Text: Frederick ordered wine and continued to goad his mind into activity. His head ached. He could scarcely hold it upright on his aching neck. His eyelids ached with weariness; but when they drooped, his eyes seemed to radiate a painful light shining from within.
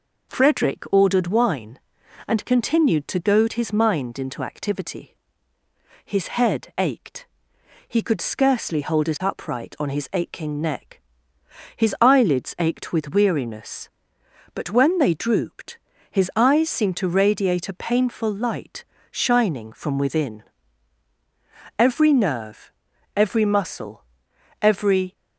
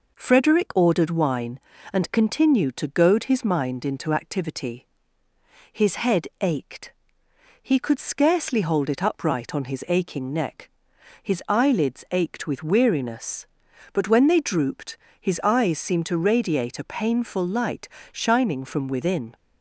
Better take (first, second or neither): second